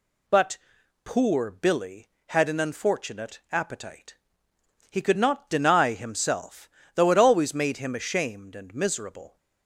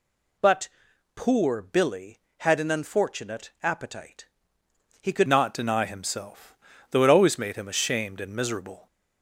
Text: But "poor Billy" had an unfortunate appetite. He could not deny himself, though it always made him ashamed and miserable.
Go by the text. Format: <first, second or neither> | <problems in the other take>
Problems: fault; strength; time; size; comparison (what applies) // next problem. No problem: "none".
first | pauses between "But" and "poor"; noticeable; at 0.6 s; 0.48 s long; noticeable in the first // changes voice at "not"; from 5.2 s on; 3.6 s long